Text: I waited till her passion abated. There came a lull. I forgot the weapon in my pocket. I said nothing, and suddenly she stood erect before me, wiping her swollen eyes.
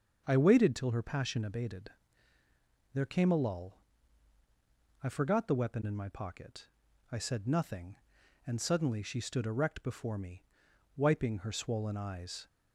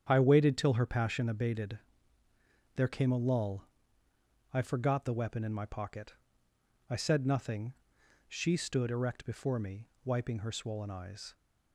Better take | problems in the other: first | starts louder than the rest; strong; until 1.1 s; 9 dB; also in the first // skips "and suddenly"; at 8.0 s

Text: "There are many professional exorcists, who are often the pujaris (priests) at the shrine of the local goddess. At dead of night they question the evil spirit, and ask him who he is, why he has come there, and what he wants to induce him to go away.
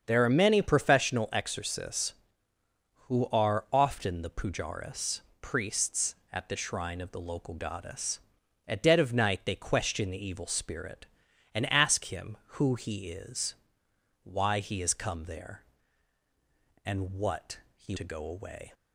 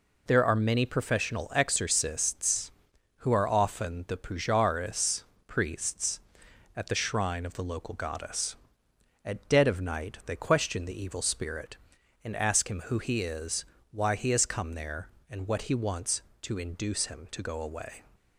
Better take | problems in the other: second | starts louder than the rest; until 1.0 s; 7 dB // pauses between "what" and "he"; slight; at 17.5 s; 0.16 s long // skips "wants to induce him"; at 17.9 s

